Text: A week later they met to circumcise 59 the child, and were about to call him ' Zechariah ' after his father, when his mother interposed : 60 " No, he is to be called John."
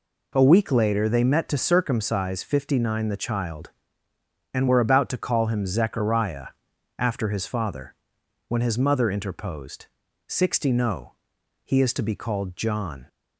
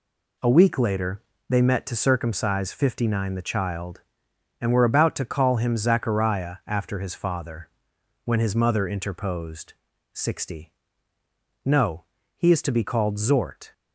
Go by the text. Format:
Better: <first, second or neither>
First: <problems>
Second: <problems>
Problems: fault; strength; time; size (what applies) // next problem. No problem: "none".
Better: first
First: none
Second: pauses between "later" and "they"; slight; at 1.2 s; 0.28 s long // says "Zort" for "John"; at 13.1 s